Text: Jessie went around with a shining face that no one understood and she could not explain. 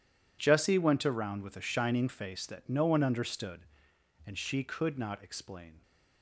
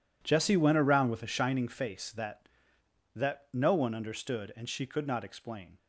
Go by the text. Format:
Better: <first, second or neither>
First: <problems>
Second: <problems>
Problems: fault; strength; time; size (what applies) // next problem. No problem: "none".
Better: first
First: none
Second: says "that" twice; at 3.1 s